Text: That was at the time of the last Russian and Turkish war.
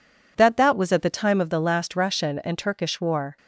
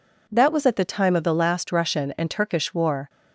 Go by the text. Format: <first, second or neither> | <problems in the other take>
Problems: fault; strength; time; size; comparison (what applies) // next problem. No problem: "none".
second | says "That" twice; at 0.5 s